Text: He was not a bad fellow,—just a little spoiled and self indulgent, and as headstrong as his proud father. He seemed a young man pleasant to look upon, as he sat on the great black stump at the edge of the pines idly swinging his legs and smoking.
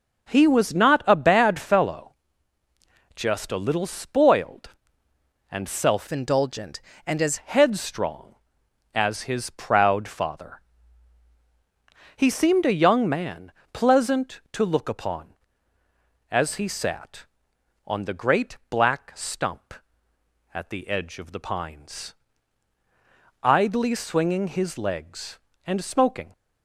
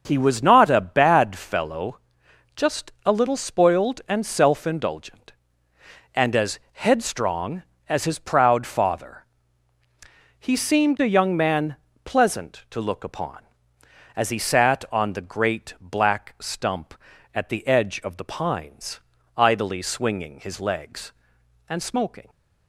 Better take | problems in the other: second | starts louder than the rest; noticeable; until 1.3 s; 6 dB; also in the second // changes voice from "indulgent" to "as"; from 6.0 to 7.3 s; 1.3 s long // pauses between "man" and "pleasant"; slight; at 13.5 s; 0.22 s long; slight in the second // pauses between "pines" and "idly"; strong; at 22.1 s; 1.3 s long; slight in the second

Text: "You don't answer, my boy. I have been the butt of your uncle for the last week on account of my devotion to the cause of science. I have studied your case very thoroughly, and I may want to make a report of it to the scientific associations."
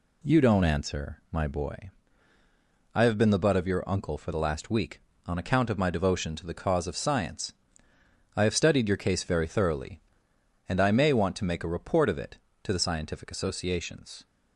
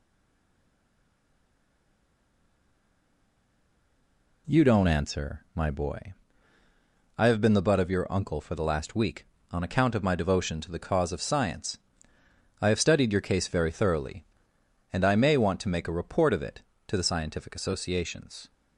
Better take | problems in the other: first | stays silent before the first word; strong; until 4.4 s; 4.4 s long

